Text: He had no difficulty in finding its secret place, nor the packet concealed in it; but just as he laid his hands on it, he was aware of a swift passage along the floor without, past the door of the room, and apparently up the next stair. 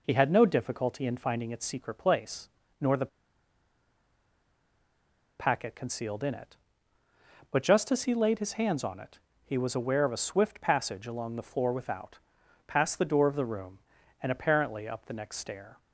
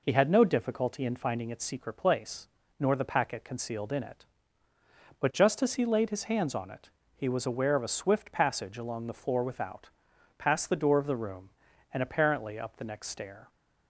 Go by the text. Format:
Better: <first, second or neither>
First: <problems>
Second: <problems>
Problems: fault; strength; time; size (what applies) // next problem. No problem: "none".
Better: second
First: pauses between "the" and "packet"; strong; at 3.0 s; 2.3 s long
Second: none